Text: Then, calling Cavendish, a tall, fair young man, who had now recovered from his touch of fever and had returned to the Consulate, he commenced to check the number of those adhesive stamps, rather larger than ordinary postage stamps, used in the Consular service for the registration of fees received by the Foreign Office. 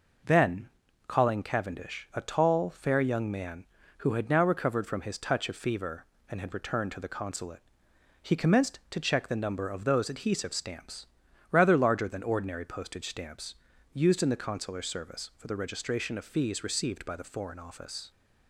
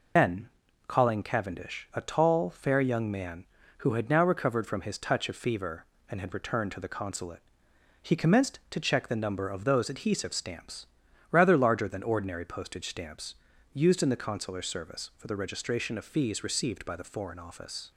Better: first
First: none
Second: loses the start of "Then"; at 0.1 s; 110 ms

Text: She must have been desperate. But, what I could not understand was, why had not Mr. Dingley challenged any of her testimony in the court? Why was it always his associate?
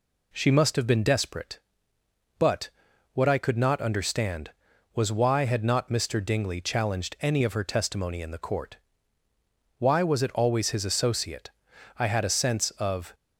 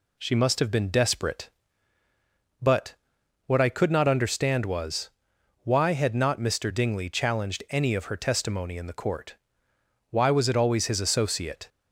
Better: second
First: goes on to say "I had a sense of"; noticeable; from 11.9 s on; 1.1 s long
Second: none

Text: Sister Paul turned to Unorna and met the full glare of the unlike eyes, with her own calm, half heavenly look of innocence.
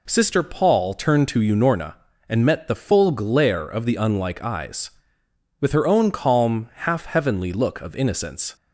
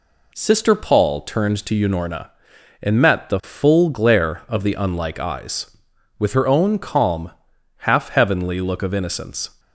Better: neither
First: none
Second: none

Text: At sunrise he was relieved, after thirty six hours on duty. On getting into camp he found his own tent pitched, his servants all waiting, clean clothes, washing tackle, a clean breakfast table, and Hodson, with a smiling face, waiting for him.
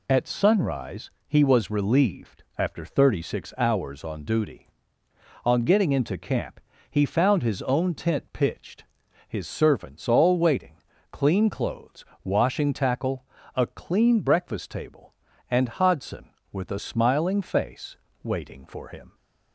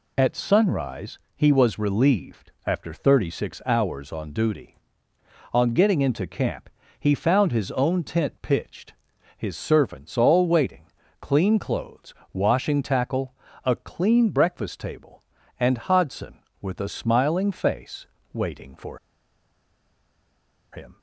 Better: first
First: pauses between "sunrise" and "he"; slight; at 1.1 s; 0.16 s long // pauses between "camp" and "he"; slight; at 6.5 s; 0.30 s long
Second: pauses between "sunrise" and "he"; slight; at 1.1 s; 0.16 s long // pauses between "camp" and "he"; slight; at 6.6 s; 0.30 s long // pauses between "for" and "him"; strong; at 18.9 s; 1.7 s long

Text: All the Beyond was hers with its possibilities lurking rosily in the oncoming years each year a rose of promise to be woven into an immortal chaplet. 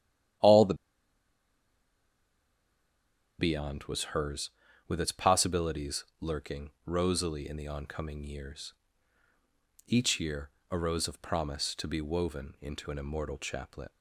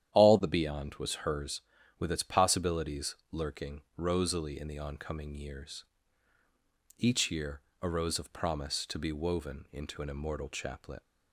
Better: second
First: starts louder than the rest; strong; until 4.0 s; 10.5 dB // pauses between "the" and "Beyond"; strong; at 0.7 s; 2.6 s long // pauses between "possibilities" and "lurking"; slight; at 6.0 s; 0.16 s long // pauses between "years" and "each"; at 8.7 s; 1.1 s long // pauses between "year" and "a"; slight; at 10.5 s; 0.18 s long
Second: starts louder than the rest; strong; until 1.1 s; 10.5 dB // pauses between "possibilities" and "lurking"; slight; at 3.1 s; 0.16 s long // pauses between "years" and "each"; at 5.8 s; 1.1 s long // pauses between "year" and "a"; slight; at 7.6 s; 0.18 s long

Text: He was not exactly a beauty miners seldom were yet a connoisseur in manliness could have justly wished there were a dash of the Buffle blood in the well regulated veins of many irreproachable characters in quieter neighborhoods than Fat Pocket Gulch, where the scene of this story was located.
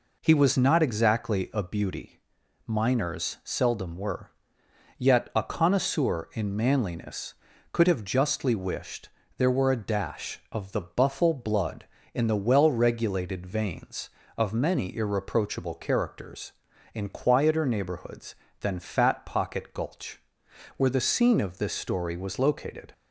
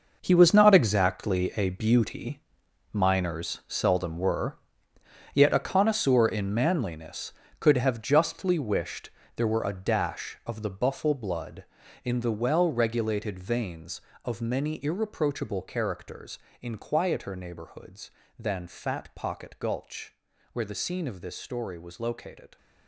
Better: first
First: pauses between "beauty" and "miners"; noticeable; at 2.1 s; 0.48 s long // pauses between "were" and "yet"; noticeable; at 4.3 s; 0.68 s long // pauses between "wished" and "there"; slight; at 9.0 s; 0.30 s long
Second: gets quieter; strong; throughout; 12 dB // pauses between "beauty" and "miners"; noticeable; at 2.4 s; 0.52 s long // pauses between "were" and "yet"; noticeable; at 4.5 s; 0.76 s long // pauses between "wished" and "there"; slight; at 9.0 s; 0.28 s long

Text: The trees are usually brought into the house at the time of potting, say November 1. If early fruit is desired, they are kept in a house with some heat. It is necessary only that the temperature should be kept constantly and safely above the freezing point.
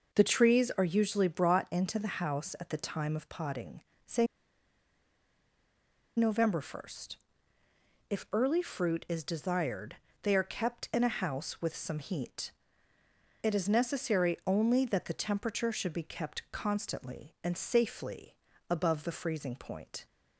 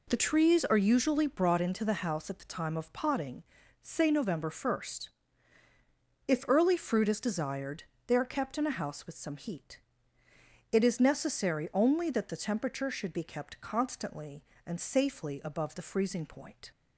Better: second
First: pauses between "say" and "November"; strong; at 4.2 s; 1.9 s long // pauses between "safely" and "above"; slight; at 18.3 s; 0.34 s long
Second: none

